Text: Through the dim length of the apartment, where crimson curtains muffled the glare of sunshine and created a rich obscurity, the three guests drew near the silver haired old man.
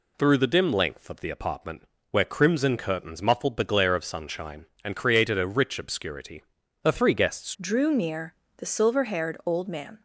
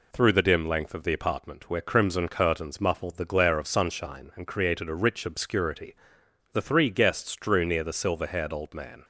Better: second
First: changes voice at "drew"; from 7.5 s on; 2.5 s long // pauses between "near" and "the"; slight; at 8.3 s; 0.22 s long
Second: none

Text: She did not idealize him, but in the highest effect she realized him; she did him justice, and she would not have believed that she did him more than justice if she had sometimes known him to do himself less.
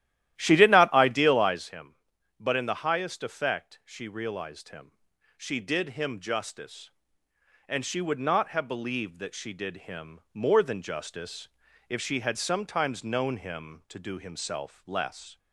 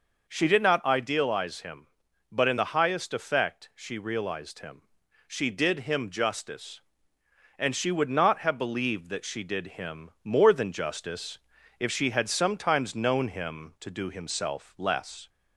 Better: second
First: starts louder than the rest; strong; until 1.7 s; 13 dB // pauses between "justice" and "if"; at 11.4 s; 0.40 s long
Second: pauses between "justice" and "if"; at 11.3 s; 0.40 s long

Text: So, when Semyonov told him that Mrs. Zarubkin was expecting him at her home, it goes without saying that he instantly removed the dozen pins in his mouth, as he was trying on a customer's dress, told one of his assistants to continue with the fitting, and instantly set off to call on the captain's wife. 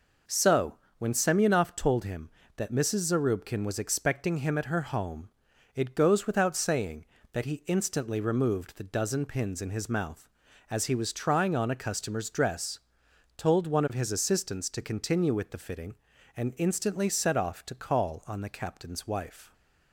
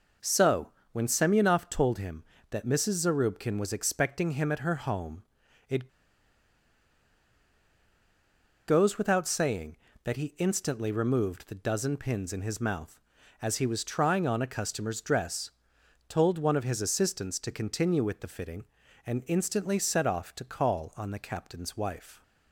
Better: first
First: none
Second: pauses between "it" and "goes"; strong; at 5.8 s; 2.7 s long

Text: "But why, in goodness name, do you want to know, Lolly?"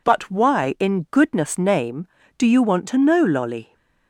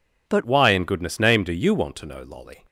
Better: first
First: none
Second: changes voice at "why"; from 0.4 s on; 2.2 s long

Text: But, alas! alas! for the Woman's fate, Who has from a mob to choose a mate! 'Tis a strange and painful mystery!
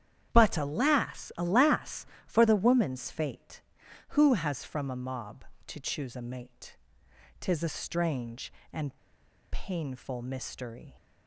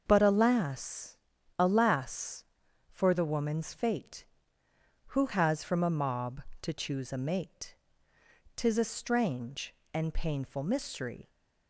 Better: second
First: starts louder than the rest; strong; until 1.3 s; 9.5 dB // pauses between "and" and "painful"; noticeable; at 8.9 s; 0.53 s long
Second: starts louder than the rest; until 1.0 s; 6.5 dB

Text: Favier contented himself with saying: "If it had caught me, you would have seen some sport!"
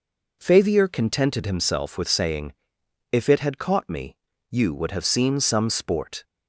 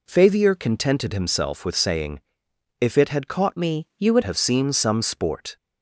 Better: first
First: none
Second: changes voice from "me" to "would"; from 3.5 to 4.2 s; 0.7 s long

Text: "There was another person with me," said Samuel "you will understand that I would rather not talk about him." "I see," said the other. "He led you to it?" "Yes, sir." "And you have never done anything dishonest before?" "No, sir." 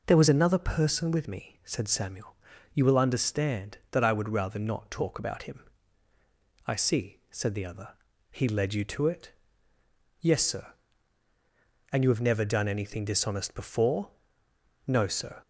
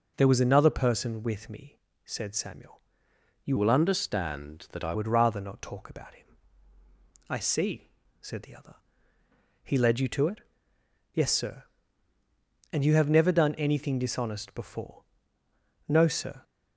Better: first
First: pauses between "Samuel" and "you"; at 2.3 s; 0.40 s long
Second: pauses between "Samuel" and "you"; noticeable; at 2.7 s; 0.64 s long // changes voice from "will" to "I"; from 3.5 to 4.9 s; 1.4 s long

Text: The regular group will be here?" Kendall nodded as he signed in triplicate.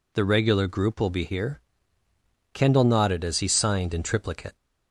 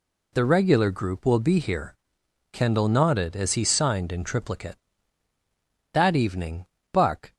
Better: first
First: none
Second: goes on to say "That evening Buck"; from 5.9 s on; 1.4 s long

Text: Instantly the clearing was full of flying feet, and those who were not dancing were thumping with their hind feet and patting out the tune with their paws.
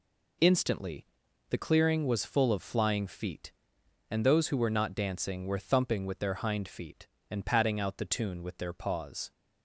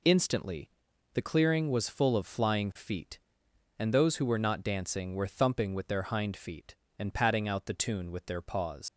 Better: first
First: pauses between "Instantly" and "the"; at 1.0 s; 0.44 s long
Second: pauses between "Instantly" and "the"; at 0.6 s; 0.44 s long // leaves "paws" unfinished; at 8.8 s; 115 ms

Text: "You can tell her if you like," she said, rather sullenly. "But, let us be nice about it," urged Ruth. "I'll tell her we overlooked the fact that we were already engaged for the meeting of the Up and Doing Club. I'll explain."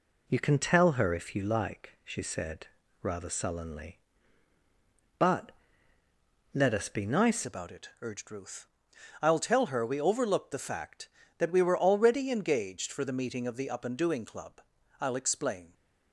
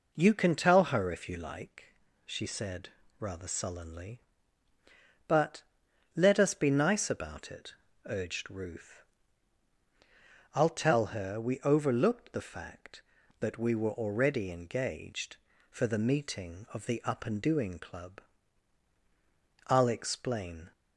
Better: second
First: changes voice at "about"; from 7.4 s on; 8.3 s long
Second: none

